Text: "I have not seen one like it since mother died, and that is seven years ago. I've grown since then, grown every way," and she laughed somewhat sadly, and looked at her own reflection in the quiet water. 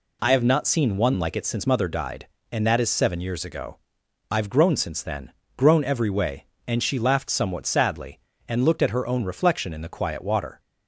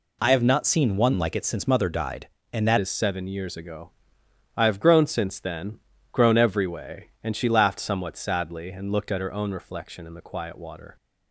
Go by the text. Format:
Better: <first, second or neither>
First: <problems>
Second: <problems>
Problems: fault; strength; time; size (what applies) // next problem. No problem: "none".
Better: first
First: none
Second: changes voice at "is"; from 2.7 s on; 8.2 s long